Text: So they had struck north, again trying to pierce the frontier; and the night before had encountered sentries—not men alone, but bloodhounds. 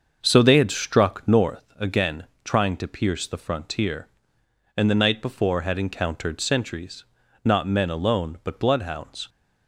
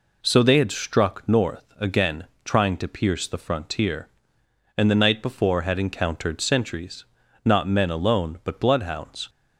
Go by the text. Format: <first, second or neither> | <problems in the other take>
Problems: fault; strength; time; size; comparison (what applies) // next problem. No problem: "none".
second | starts louder than the rest; until 1.6 s; 6.5 dB // pauses between "again" and "trying"; slight; at 2.2 s; 0.20 s long; slight in the second